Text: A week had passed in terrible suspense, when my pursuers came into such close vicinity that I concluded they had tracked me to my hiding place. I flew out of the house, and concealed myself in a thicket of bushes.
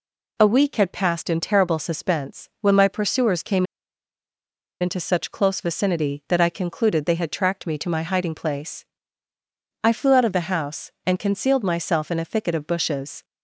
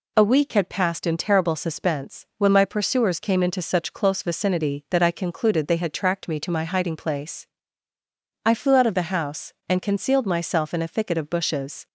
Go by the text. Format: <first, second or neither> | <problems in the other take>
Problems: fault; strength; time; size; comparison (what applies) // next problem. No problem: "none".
second | pauses between "came" and "into"; at 3.6 s; 1.1 s long